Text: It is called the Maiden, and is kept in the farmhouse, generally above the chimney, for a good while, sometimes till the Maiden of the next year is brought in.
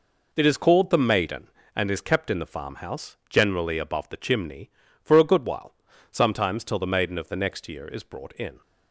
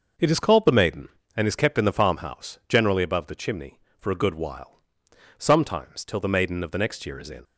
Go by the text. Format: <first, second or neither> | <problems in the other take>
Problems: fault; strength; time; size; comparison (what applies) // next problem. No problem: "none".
first | starts louder than the rest; noticeable; until 1.4 s; 6 dB // skips "brought"; at 7.2 s